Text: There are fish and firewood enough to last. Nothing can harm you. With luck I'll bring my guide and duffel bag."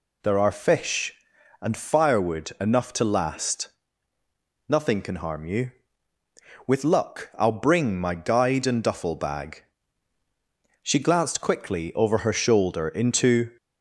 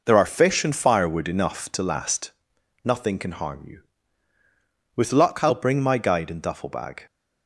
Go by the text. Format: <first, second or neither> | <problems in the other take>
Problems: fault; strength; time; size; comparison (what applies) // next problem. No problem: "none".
second | goes on to say "She glanced quickly over her shoulder into"; strong; from 10.8 s on; 2.6 s long